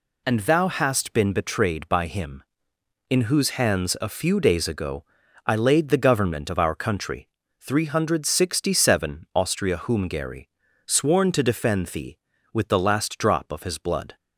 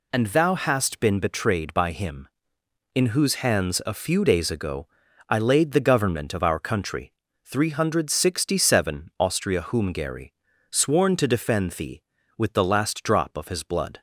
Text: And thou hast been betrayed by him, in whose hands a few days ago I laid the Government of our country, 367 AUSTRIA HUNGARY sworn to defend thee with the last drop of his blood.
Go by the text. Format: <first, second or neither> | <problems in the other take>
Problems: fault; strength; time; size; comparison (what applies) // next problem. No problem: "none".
neither | pauses between "ago" and "I"; the same in both // pauses between "HUNGARY" and "sworn"; slight; the same in both